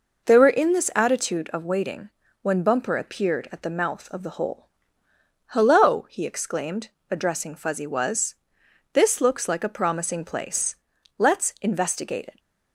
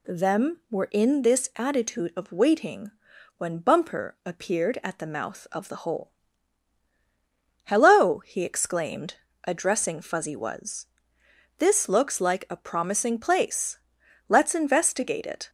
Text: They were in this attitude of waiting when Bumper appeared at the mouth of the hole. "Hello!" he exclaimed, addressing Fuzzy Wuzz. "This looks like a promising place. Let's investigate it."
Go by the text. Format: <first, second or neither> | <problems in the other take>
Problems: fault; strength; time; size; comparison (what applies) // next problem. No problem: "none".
first | says "Them" for "They"; at 0.0 s // pauses between "waiting" and "when"; noticeable; at 2.9 s; 0.46 s long; slight in the first